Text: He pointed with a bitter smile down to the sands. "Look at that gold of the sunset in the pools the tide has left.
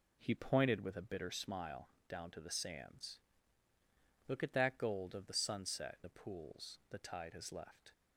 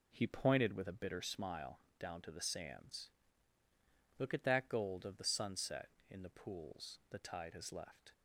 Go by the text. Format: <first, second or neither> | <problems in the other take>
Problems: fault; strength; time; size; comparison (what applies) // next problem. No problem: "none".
second | pauses between "smile" and "down"; slight; at 1.8 s; 0.22 s long; slight in the second // skips "in"; at 6.0 s